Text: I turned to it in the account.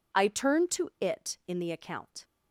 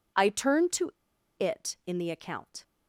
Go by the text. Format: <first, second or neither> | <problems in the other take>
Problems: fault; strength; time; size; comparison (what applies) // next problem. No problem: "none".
first | pauses between "to" and "it"; noticeable; at 0.9 s; 0.48 s long